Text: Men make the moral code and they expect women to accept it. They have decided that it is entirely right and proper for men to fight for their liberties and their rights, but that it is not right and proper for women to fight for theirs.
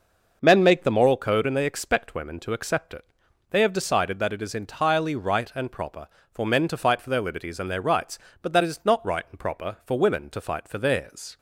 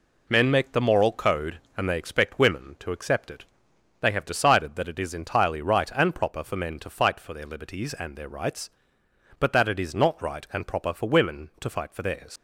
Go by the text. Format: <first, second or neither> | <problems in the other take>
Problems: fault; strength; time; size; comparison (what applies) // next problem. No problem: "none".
first | leaves "theirs" unfinished; at 12.3 s; 95 ms